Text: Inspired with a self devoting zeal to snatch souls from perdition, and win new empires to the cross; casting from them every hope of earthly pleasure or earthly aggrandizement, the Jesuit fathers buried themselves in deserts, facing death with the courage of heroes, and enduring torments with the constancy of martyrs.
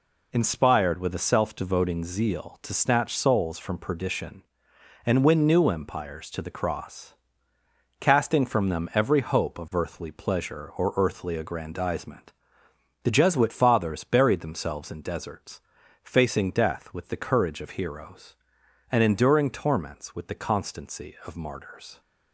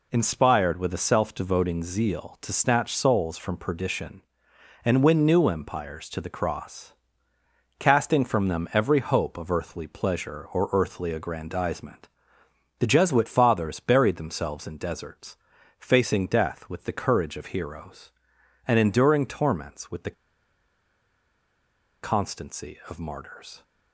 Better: first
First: none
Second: pauses between "the" and "constancy"; strong; at 20.1 s; 1.8 s long

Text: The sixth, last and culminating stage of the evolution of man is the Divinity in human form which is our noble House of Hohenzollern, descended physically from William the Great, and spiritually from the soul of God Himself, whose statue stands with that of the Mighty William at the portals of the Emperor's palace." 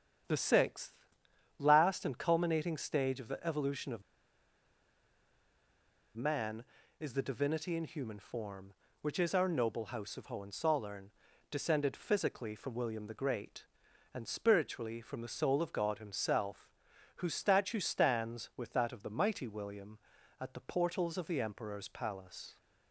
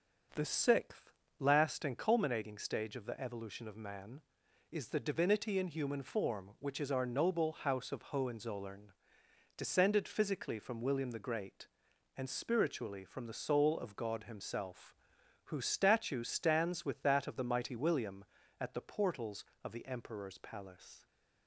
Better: second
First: starts louder than the rest; strong; until 1.8 s; 8.5 dB // pauses between "of" and "man"; strong; at 4.0 s; 2.1 s long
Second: none

